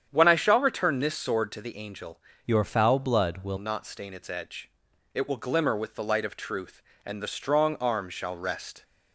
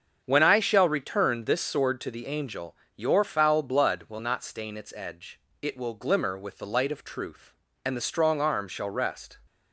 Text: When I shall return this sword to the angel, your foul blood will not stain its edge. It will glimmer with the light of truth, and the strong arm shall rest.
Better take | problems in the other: second | starts louder than the rest; strong; until 1.1 s; 8.5 dB; also in the second // changes voice from "your" to "will"; from 2.4 to 3.5 s; 1.1 s long

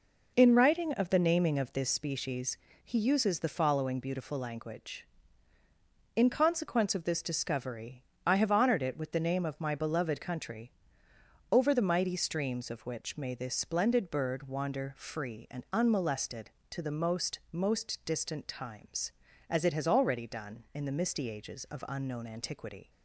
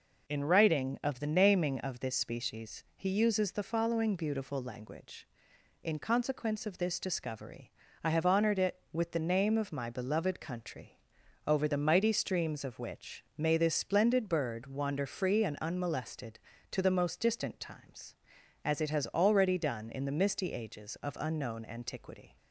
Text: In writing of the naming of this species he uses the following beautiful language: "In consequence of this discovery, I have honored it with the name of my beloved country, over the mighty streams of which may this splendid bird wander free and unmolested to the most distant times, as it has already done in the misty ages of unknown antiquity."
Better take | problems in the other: second | pauses between "species" and "he"; slight; at 2.5 s; 0.26 s long // says "most" twice; at 17.5 s

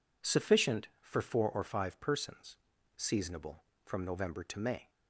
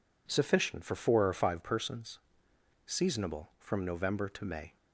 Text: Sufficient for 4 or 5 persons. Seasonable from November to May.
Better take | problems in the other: neither | none

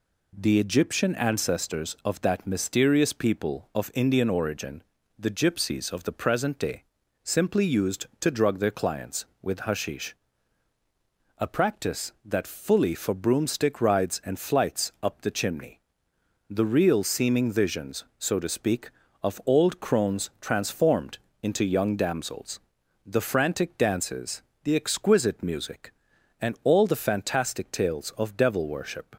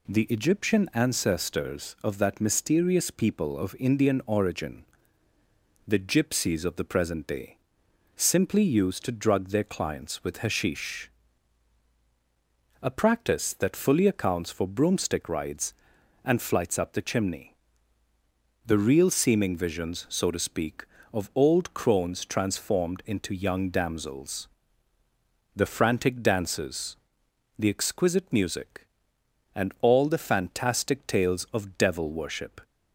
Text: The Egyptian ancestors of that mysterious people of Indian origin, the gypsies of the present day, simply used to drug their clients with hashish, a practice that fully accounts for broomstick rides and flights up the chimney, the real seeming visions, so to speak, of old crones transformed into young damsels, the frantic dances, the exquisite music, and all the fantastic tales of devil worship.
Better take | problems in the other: second | skips "accounts"; at 12.9 s // pauses between "transformed" and "into"; slight; at 21.1 s; 0.26 s long

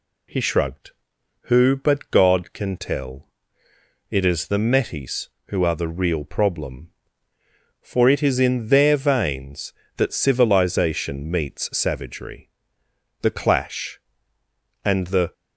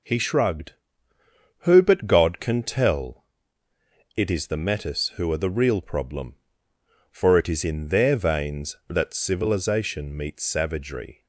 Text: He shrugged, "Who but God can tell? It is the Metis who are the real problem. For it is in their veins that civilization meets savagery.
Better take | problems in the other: second | goes on to say "The clash and the"; strong; from 13.2 s on; 2.1 s long

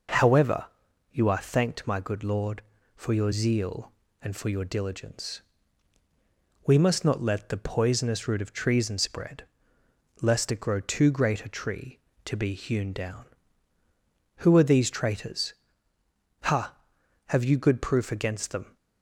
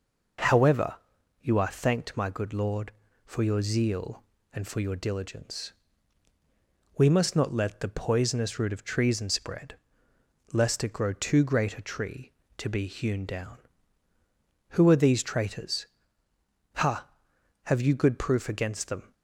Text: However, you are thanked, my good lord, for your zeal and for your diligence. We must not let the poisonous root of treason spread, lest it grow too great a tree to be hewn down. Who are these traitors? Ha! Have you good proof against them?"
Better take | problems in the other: neither | none

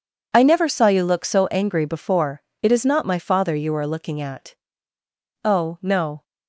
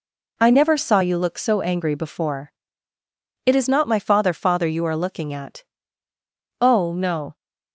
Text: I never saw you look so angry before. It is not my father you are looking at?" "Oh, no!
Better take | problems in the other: first | says "father" twice; at 4.3 s

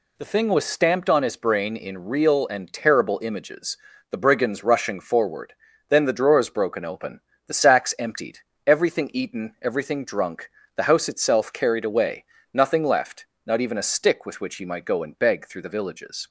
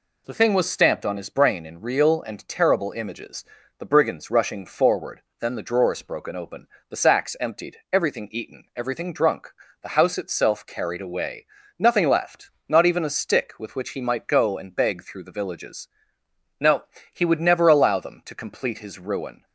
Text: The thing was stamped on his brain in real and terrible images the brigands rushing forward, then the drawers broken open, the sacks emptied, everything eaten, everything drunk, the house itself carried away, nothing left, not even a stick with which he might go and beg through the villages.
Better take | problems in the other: first | pauses between "images" and "the"; slight; at 3.4 s; 0.34 s long; slight in the first // goes on to say "No he would never allow them to complete his ruin"; strong; from 16.5 s on; 2.8 s long

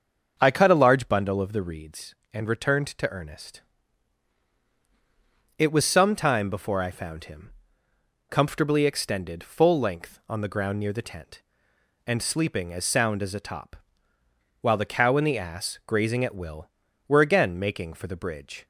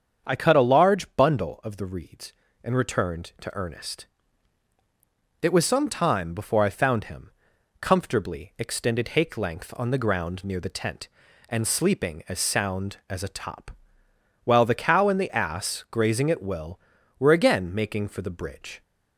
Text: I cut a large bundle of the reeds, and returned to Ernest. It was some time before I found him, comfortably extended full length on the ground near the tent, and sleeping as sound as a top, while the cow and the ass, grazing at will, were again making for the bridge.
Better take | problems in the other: first | starts louder than the rest; strong; until 1.3 s; 7.5 dB; also in the first // says "hake" for "full"; at 9.0 s

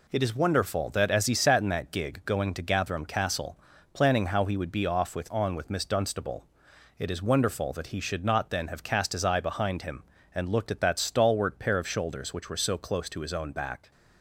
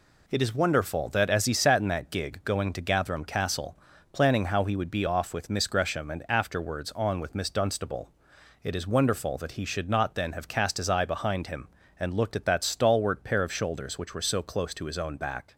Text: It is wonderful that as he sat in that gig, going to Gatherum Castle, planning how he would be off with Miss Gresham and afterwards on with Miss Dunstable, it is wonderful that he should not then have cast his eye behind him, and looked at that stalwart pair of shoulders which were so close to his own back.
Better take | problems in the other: second | skips "Miss Gresham and afterwards"; at 5.3 s

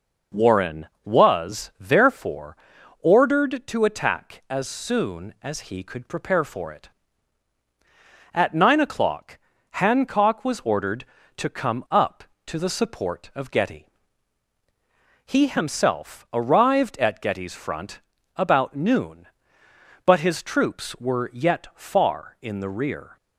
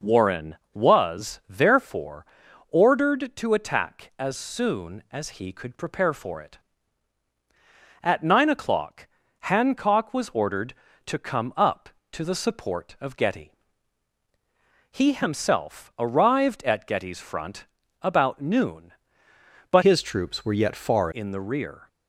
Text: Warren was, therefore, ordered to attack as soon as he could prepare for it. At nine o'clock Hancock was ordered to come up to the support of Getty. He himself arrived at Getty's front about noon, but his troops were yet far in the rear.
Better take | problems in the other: first | pauses between "o'clock" and "Hancock"; slight; at 9.0 s; 0.34 s long; slight in the first // pauses between "front" and "about"; slight; at 17.6 s; 0.36 s long; slight in the first // changes voice from "his" to "far"; from 19.8 to 21.0 s; 1.2 s long

